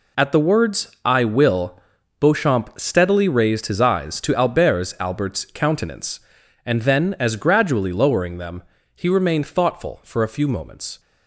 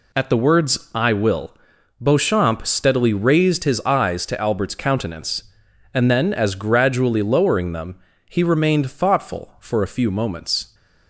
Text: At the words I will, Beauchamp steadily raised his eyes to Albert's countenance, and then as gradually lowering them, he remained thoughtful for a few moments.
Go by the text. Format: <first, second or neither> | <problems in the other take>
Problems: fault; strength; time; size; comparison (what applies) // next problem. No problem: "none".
second | says "Albert's" twice; at 4.9 s